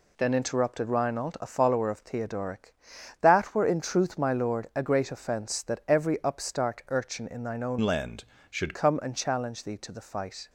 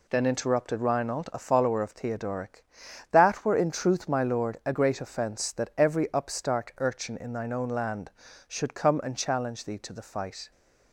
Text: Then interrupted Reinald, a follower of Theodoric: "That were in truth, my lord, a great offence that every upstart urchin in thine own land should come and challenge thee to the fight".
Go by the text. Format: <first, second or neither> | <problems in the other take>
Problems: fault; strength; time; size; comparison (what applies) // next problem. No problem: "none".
second | changes voice from "land" to "should"; from 7.7 to 8.7 s; 1.0 s long